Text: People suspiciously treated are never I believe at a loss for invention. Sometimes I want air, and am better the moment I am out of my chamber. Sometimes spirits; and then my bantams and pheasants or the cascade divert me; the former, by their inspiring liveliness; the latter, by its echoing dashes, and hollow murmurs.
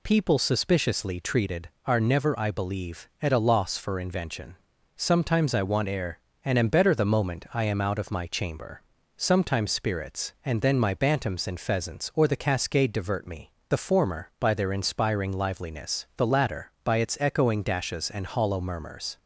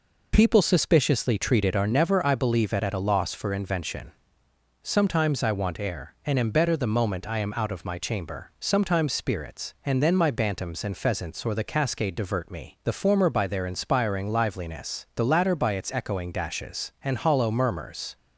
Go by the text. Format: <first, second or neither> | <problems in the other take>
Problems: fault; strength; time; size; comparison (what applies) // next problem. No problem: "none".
first | says "at" twice; at 2.8 s